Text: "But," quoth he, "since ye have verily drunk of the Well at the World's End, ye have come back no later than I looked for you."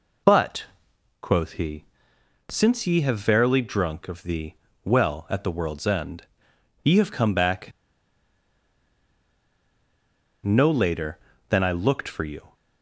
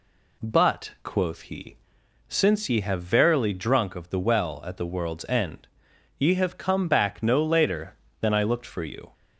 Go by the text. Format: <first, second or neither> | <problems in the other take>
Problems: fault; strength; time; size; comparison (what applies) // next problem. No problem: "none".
second | pauses between "the" and "Well"; slight; at 4.5 s; 0.32 s long // pauses between "back" and "no"; strong; at 7.7 s; 2.7 s long